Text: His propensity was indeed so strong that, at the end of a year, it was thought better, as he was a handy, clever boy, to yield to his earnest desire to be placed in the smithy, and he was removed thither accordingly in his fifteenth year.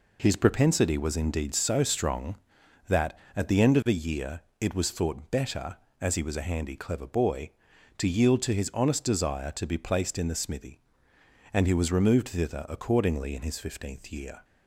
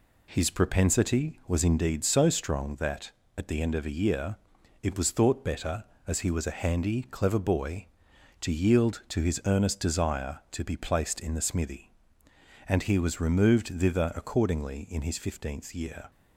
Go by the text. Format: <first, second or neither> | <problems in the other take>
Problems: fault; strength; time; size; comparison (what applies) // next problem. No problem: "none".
second | says "honest" for "earnest"; at 8.7 s